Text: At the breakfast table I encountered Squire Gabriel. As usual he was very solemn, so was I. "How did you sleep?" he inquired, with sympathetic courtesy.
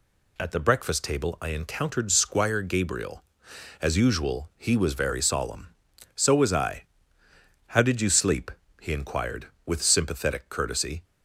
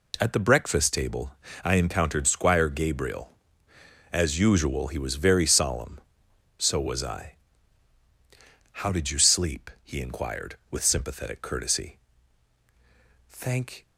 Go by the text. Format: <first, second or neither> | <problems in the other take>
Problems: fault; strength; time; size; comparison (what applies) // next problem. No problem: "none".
first | pauses between "table" and "I"; slight; at 1.3 s; 0.28 s long // goes on to say "Thank"; from 13.2 s on; 0.58 s long